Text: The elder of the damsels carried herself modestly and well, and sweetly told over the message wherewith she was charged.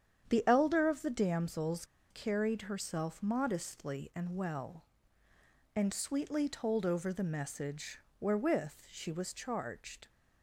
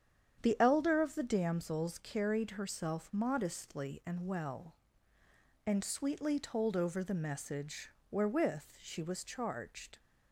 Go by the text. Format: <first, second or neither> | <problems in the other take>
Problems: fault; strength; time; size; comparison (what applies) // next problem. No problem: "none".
second | starts louder than the rest; strong; until 1.3 s; 8.5 dB; strong in the second // pauses between "damsels" and "carried"; slight; at 1.8 s; 0.26 s long // pauses between "message" and "wherewith"; slight; at 8.0 s; 0.18 s long; slight in the second // pauses between "wherewith" and "she"; slight; at 8.7 s; 0.18 s long; slight in the second